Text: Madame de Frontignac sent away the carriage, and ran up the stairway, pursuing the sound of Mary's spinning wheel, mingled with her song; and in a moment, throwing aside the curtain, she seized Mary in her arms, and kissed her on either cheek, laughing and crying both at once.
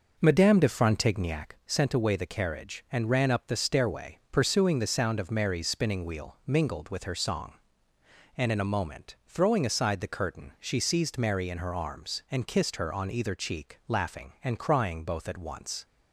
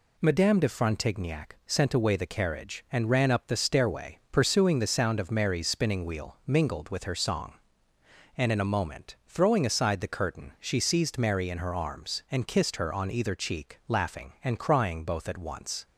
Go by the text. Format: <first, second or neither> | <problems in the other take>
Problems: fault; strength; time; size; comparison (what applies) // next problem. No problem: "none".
second | starts louder than the rest; noticeable; until 1.6 s; 5.5 dB